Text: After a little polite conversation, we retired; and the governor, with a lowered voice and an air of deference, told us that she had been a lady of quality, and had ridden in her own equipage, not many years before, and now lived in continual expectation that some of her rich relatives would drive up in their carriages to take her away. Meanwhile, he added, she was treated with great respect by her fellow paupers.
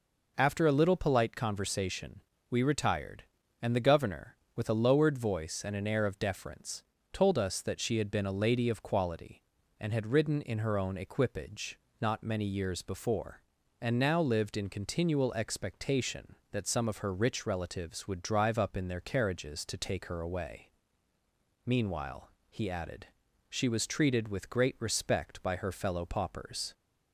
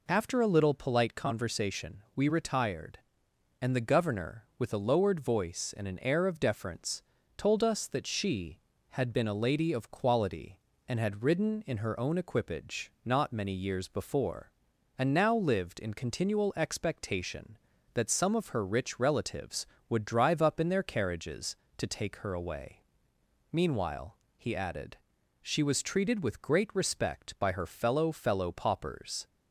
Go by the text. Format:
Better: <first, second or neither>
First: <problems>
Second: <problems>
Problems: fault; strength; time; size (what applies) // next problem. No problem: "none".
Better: first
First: none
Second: says "fellow" twice; at 28.1 s